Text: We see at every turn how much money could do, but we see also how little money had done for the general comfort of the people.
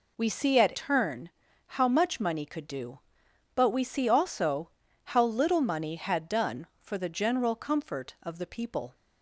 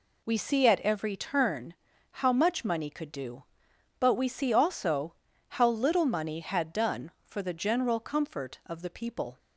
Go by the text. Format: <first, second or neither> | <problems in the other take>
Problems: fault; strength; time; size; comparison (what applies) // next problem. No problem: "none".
second | skips "every"; at 0.7 s // pauses between "turn" and "how"; at 1.2 s; 0.38 s long; also in the second // pauses between "also" and "how"; slight; at 4.7 s; 0.34 s long; slight in the second